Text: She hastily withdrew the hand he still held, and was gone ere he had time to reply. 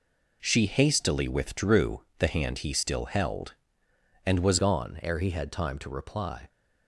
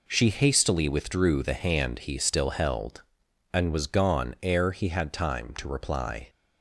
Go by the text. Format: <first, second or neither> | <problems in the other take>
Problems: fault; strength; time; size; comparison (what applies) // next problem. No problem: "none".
second | changes voice at "gone"; from 4.5 s on; 1.9 s long